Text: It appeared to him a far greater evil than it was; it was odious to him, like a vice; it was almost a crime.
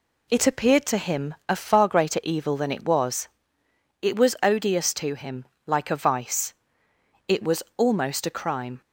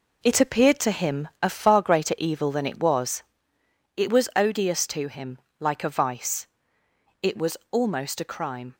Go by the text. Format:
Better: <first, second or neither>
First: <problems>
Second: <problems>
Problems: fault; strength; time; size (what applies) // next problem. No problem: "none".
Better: first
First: none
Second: gets quieter; strong; throughout; 7.5 dB